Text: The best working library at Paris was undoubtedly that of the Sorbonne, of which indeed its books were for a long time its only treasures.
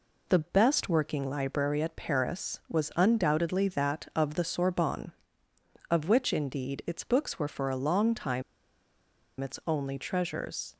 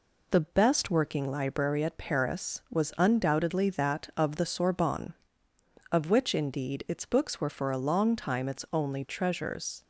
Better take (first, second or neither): second